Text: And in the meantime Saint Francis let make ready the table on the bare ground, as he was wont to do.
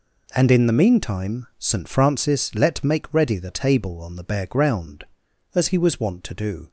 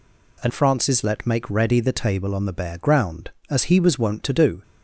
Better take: first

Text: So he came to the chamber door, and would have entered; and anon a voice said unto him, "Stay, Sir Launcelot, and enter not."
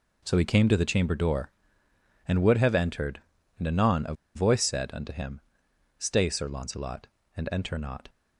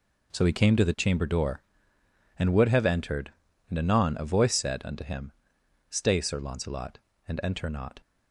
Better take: second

